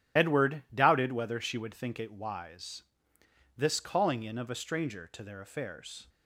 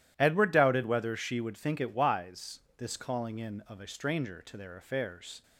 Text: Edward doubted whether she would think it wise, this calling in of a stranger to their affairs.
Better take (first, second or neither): second